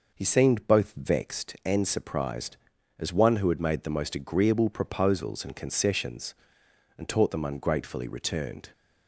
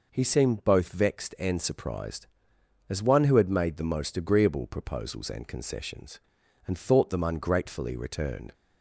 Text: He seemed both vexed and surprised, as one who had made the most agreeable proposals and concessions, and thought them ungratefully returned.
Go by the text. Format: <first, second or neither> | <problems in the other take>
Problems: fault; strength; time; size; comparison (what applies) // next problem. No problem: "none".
second | says "taught" for "thought"; at 7.0 s